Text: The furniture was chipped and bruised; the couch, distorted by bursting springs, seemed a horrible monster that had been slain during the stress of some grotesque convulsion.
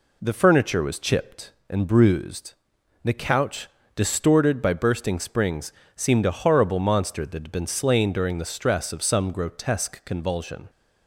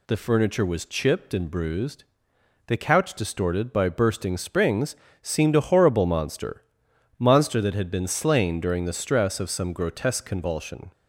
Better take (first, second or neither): first